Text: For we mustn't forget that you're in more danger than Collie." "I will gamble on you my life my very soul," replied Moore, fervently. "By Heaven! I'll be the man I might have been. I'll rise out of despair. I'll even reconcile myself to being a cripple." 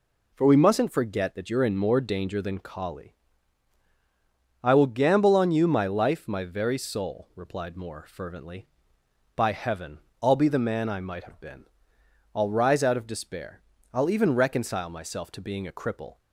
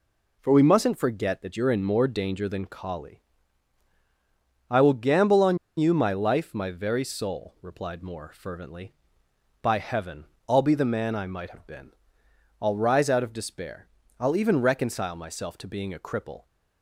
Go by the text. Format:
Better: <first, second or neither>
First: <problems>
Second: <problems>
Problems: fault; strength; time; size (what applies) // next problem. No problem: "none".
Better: first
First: none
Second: pauses between "on" and "you"; slight; at 5.5 s; 0.20 s long